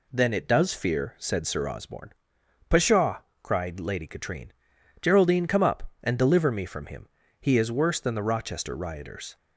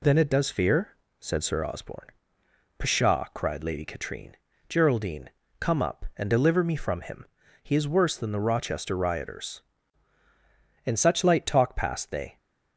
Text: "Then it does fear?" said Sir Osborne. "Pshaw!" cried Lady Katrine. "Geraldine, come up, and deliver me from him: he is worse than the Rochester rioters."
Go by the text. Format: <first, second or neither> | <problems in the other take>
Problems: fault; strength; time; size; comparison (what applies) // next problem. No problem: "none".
first | goes on to say "In such light talk passed they"; from 10.8 s on; 1.5 s long